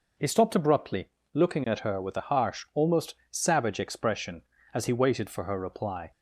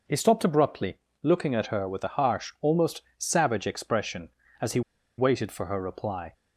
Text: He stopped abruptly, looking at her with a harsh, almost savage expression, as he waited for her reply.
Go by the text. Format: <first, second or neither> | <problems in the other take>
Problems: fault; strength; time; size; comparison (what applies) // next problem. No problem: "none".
first | pauses between "almost" and "savage"; slight; at 3.0 s; 0.16 s long; slight in the first // pauses between "he" and "waited"; at 4.8 s; 0.37 s long